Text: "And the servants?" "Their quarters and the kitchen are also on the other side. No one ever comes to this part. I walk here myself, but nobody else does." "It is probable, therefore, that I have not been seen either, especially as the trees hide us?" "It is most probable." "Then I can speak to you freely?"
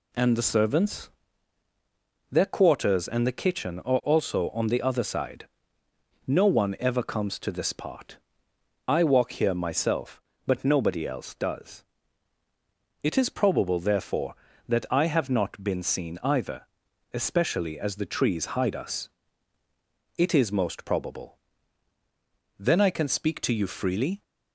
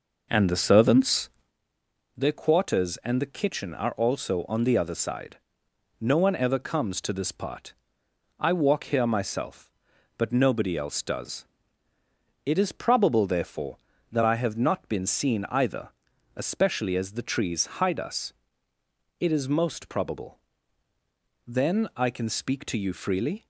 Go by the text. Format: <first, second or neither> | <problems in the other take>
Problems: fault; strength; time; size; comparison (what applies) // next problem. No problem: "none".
first | starts louder than the rest; noticeable; until 1.5 s; 5 dB